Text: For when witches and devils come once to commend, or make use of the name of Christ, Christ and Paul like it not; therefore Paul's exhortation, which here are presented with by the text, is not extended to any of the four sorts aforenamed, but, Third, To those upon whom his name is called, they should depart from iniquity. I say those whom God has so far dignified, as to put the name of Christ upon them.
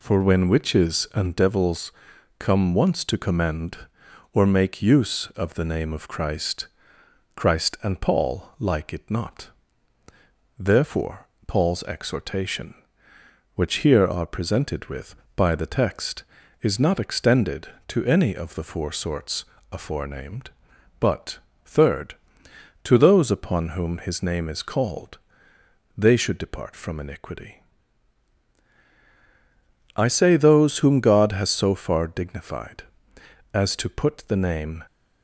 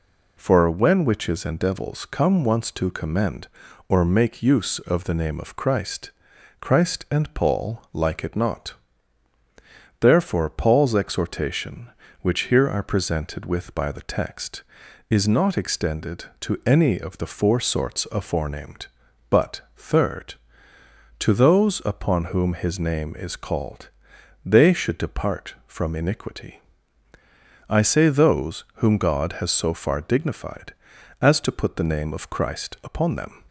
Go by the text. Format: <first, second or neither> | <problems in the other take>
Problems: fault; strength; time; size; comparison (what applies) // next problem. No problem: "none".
second | pauses between "devils" and "come"; noticeable; at 1.9 s; 0.48 s long // pauses between "therefore" and "Paul's"; slight; at 11.2 s; 0.18 s long // pauses between "sorts" and "aforenamed"; slight; at 19.4 s; 0.28 s long // stops before "of Christ upon them"; at 34.8 s